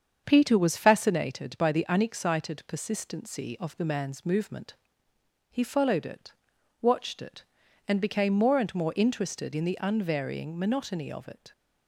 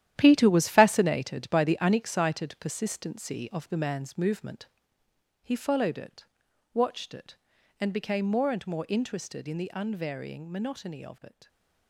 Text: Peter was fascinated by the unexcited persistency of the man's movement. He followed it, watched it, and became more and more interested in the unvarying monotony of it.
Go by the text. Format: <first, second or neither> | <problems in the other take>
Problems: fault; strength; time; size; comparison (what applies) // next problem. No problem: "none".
first | gets quieter; strong; throughout; 11 dB // starts louder than the rest; strong; until 1.1 s; 11.5 dB; strong in the first